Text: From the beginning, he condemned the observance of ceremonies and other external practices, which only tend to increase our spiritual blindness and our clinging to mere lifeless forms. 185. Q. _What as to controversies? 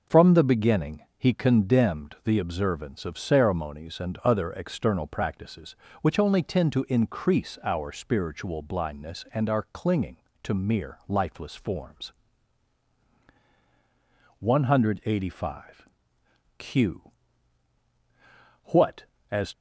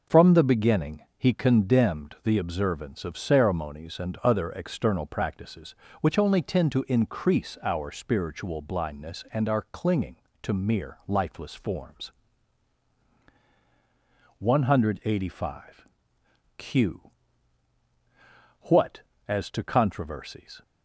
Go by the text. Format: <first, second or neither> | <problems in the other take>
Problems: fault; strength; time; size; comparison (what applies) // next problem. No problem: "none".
second | stops before "to controversies"; at 19.5 s